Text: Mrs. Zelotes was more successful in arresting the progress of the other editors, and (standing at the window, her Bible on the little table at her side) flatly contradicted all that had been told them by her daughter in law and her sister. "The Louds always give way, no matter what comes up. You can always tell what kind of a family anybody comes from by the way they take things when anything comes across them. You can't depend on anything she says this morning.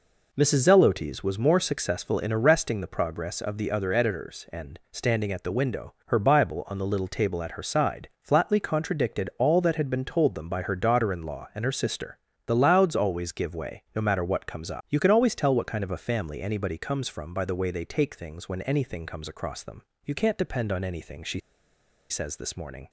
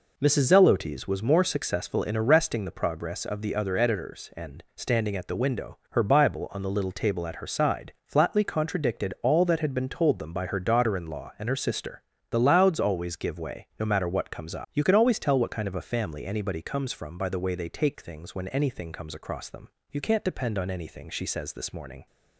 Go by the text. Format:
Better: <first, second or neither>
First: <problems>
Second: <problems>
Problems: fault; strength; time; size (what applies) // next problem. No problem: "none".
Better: second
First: pauses between "she" and "says"; noticeable; at 21.3 s; 0.70 s long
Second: none